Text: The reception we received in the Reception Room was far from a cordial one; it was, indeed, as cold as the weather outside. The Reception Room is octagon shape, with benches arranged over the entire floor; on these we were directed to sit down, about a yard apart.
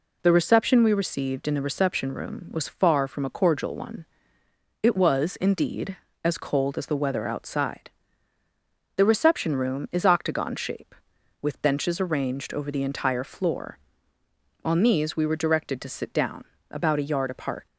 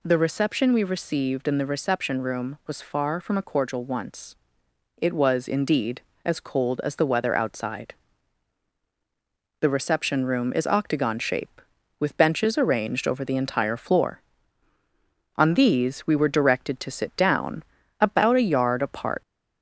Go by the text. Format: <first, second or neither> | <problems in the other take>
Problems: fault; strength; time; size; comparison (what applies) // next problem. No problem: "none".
first | says "once" for "one"; at 3.8 s